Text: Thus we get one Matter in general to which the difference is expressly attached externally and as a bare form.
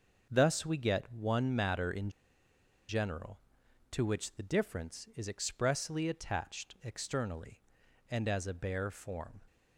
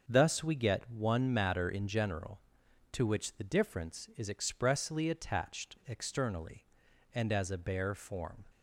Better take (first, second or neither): second